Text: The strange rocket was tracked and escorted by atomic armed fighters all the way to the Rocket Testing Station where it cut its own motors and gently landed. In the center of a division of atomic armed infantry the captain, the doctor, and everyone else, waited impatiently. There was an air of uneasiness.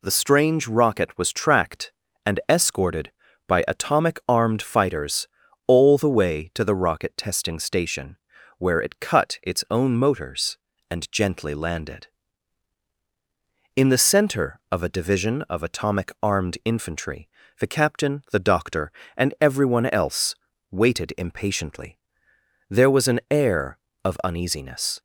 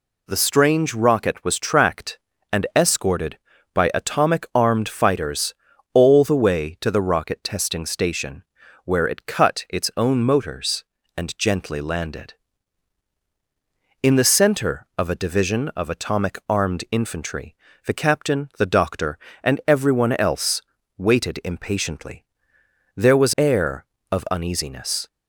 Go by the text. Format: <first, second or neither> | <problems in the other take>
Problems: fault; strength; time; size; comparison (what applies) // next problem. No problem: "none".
first | pauses between "fighters" and "all"; at 5.5 s; 0.40 s long; also in the first // pauses between "Station" and "where"; at 8.4 s; 0.40 s long; also in the first // pauses between "infantry" and "the"; slight; at 17.5 s; 0.28 s long; slight in the first // skips "an"; at 23.3 s